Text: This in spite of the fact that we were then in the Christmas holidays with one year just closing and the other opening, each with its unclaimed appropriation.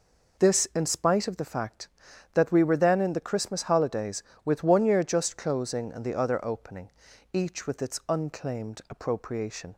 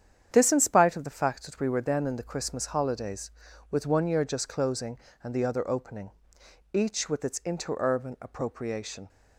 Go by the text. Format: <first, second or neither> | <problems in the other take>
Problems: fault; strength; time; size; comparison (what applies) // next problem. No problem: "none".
first | starts louder than the rest; strong; until 1.3 s; 9 dB // says "interurban" for "unclaimed"; at 7.4 s